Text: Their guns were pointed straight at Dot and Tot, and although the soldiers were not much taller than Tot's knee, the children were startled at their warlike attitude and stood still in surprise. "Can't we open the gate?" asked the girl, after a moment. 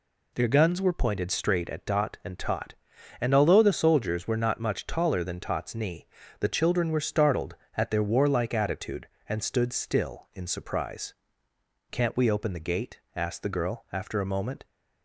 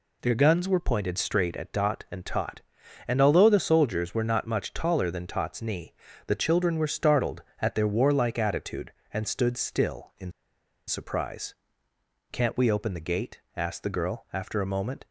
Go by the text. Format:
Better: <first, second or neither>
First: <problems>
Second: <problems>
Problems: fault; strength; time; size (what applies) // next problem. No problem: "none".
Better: first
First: none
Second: pauses between "in" and "surprise"; noticeable; at 10.3 s; 0.56 s long